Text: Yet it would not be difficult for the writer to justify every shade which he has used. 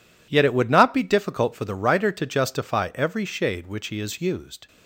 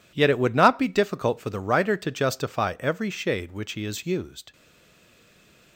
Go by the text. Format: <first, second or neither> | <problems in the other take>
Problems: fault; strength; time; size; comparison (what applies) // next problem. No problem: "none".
first | stays silent after the last word; noticeable; from 4.5 s on; 1.2 s long